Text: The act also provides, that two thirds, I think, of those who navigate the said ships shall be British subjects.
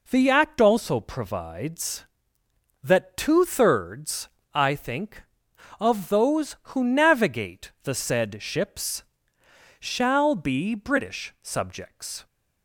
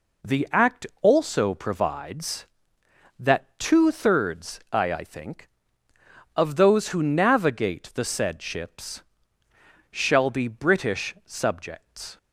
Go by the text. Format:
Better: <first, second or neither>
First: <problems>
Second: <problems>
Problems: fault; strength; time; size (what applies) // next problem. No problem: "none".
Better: first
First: pauses between "ships" and "shall"; noticeable; at 9.0 s; 0.76 s long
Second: pauses between "act" and "also"; slight; at 0.8 s; 0.16 s long // says "I" twice; at 4.9 s // pauses between "ships" and "shall"; noticeable; at 9.0 s; 0.90 s long